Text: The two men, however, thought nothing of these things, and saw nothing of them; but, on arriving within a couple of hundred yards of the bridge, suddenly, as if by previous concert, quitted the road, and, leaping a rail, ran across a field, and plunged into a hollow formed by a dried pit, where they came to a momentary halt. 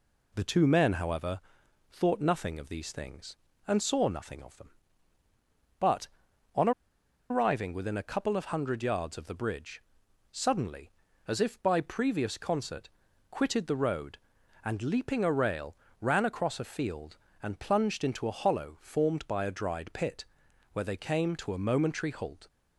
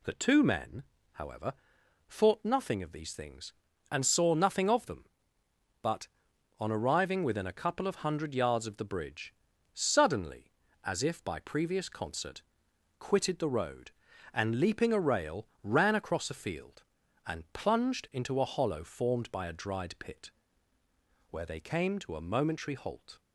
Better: second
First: pauses between "on" and "arriving"; noticeable; at 6.7 s; 0.59 s long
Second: none

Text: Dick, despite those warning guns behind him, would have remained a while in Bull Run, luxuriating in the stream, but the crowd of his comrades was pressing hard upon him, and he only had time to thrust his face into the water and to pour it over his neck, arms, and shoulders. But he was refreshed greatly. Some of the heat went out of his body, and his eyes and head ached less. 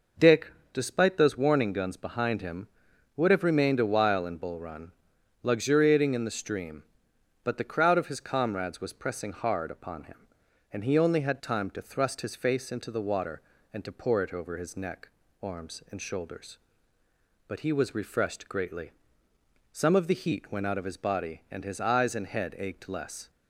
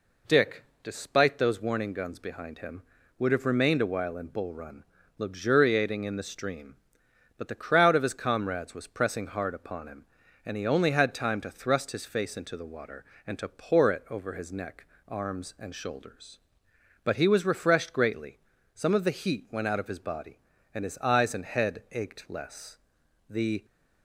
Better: first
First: none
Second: goes on to say "The"; slight; from 23.2 s on; 0.36 s long

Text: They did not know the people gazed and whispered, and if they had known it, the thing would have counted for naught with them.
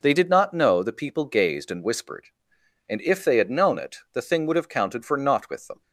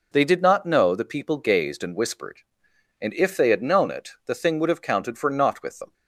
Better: neither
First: none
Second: none

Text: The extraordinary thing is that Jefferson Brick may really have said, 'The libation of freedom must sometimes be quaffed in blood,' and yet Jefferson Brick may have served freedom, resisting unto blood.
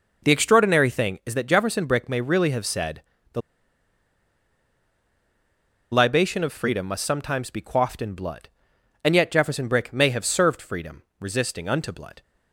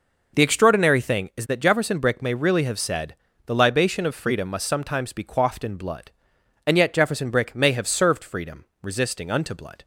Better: second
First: pauses between "The" and "libation"; strong; at 3.4 s; 2.5 s long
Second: none

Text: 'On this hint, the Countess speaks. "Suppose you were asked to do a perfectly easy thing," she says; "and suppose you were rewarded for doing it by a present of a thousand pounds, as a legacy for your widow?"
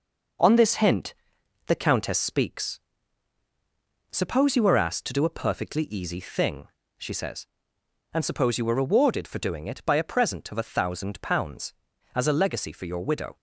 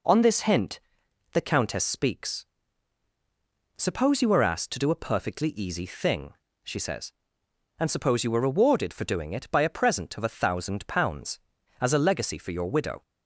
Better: second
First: gets quieter; noticeable; throughout; 4.5 dB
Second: none

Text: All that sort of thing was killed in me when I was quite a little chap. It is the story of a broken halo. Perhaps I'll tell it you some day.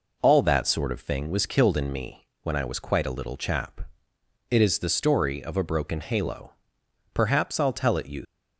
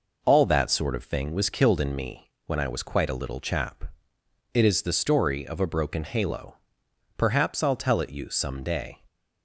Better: second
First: pauses between "me" and "when"; slight; at 2.2 s; 0.16 s long // stops before "some day"; at 8.2 s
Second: pauses between "me" and "when"; slight; at 2.2 s; 0.16 s long

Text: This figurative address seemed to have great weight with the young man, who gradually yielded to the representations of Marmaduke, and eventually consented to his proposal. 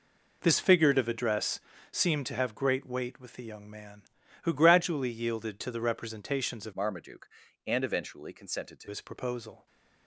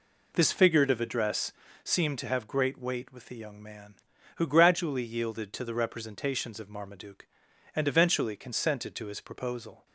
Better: second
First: pauses between "address" and "seemed"; slight; at 1.5 s; 0.32 s long // changes voice from "Marmaduke" to "to"; from 6.7 to 8.8 s; 2.1 s long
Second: pauses between "address" and "seemed"; slight; at 1.5 s; 0.32 s long

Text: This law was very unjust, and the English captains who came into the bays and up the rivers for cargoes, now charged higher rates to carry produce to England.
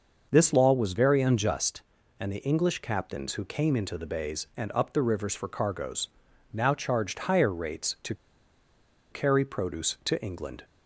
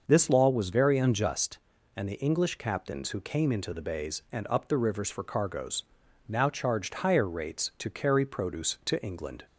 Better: second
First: starts louder than the rest; noticeable; until 1.3 s; 6 dB // pauses between "to" and "carry"; noticeable; at 8.1 s; 0.96 s long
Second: starts louder than the rest; noticeable; until 1.0 s; 6 dB

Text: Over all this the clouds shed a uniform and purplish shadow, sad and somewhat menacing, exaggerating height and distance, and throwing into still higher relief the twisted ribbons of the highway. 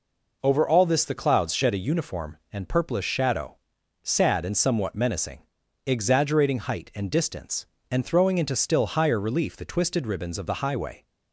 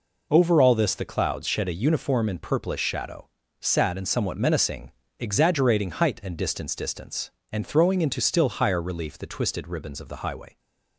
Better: first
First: none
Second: says "distance" twice; at 6.7 s

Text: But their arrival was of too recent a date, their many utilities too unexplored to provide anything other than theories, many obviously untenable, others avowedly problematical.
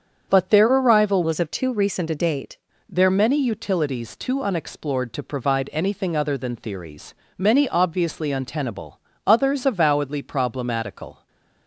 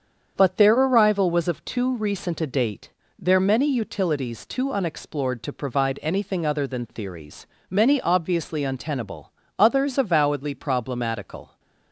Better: second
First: starts louder than the rest; strong; until 1.3 s; 7.5 dB // changes voice from "was" to "date"; from 1.2 to 2.5 s; 1.3 s long // stays silent after the last word; slight; from 11.1 s on; 0.5 s long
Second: starts louder than the rest; strong; until 1.3 s; 7.5 dB

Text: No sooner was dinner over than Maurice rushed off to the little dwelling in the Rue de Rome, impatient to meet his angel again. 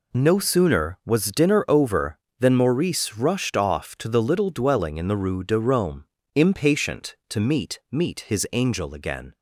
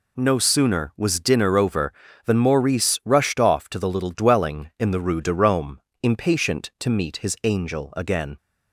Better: second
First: says "meet" twice; at 7.9 s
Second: none

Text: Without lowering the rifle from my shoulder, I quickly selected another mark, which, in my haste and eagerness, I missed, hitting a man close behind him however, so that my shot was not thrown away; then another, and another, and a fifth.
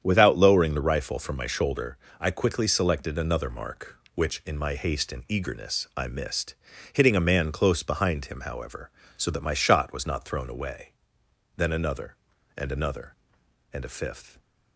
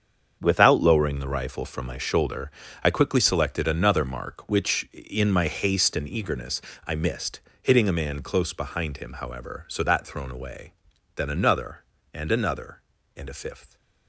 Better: first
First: starts louder than the rest; strong; until 1.0 s; 8.5 dB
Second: starts louder than the rest; strong; until 1.4 s; 7 dB // skips "my shot was not"; at 10.0 s

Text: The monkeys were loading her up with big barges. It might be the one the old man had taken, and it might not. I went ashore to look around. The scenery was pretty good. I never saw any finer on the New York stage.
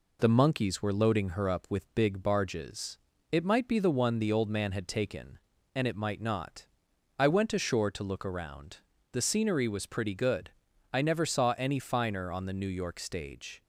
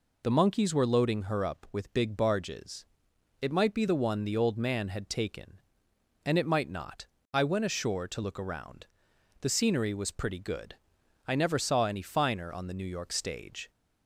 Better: neither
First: none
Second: none

